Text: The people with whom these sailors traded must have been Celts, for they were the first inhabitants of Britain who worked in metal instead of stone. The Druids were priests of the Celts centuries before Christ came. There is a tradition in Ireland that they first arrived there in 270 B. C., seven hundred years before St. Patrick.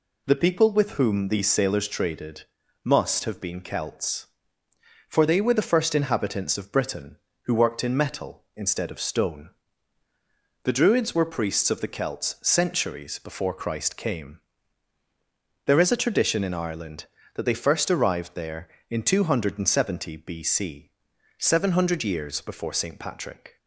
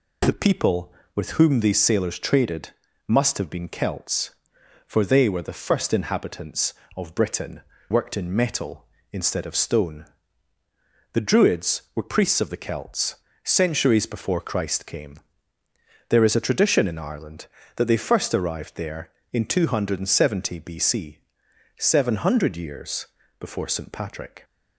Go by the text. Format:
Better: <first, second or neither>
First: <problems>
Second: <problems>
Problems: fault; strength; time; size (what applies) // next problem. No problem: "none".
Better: first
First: pauses between "traded" and "must"; at 2.4 s; 0.38 s long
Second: pauses between "traded" and "must"; at 2.6 s; 0.38 s long // skips "who"; at 7.7 s // pauses between "Celts" and "centuries"; slight; at 13.1 s; 0.28 s long // pauses between "years" and "before"; slight; at 23.0 s; 0.34 s long